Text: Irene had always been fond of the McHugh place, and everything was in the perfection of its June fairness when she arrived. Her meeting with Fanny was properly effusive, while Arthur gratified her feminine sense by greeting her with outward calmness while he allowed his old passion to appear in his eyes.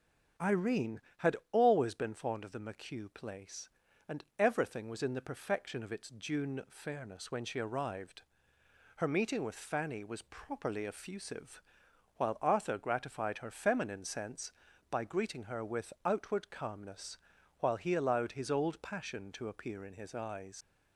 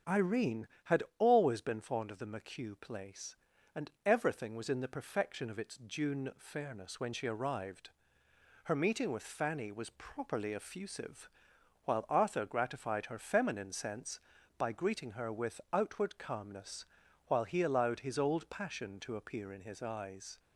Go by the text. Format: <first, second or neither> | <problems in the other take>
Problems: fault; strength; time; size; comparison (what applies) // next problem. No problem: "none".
second | starts louder than the rest; strong; until 1.7 s; 7.5 dB; strong in the second // pauses between "had" and "always"; slight; at 1.3 s; 0.16 s long; slight in the second // pauses between "calmness" and "while"; at 17.1 s; 0.42 s long; also in the second // leaves "eyes" unfinished; at 20.6 s; 105 ms